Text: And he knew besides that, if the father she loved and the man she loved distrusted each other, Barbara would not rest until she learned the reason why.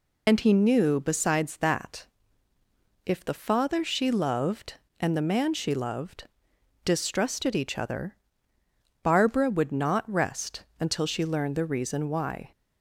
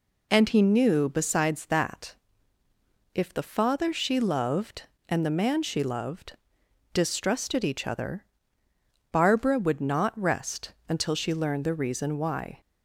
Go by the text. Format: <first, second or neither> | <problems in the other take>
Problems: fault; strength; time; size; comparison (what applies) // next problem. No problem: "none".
second | loses the start of "And"; at 0.2 s; 50 ms // pauses between "loved" and "distrusted"; noticeable; at 6.2 s; 0.58 s long; noticeable in the second // pauses between "rest" and "until"; slight; at 10.6 s; 0.16 s long; slight in the second